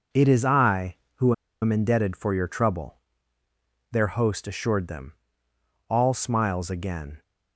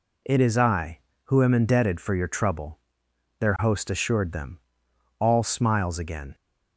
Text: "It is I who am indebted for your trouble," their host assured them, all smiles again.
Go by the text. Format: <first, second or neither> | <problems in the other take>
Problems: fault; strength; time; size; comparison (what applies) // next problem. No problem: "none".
second | pauses between "who" and "am"; slight; at 1.3 s; 0.28 s long